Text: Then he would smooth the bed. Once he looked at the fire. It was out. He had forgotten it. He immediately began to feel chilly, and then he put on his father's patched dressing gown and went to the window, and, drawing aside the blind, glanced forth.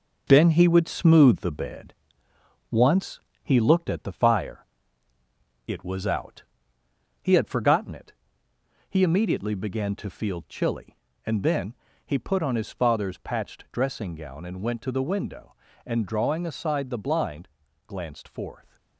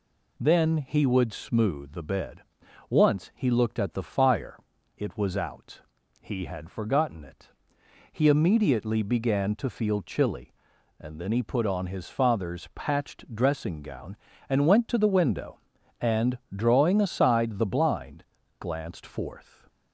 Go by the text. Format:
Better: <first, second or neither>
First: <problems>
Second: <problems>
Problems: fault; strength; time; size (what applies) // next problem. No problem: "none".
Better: second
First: gets quieter; noticeable; throughout; 6 dB // pauses between "Once" and "he"; slight; at 3.1 s; 0.24 s long // pauses between "then" and "he"; slight; at 11.7 s; 0.30 s long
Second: none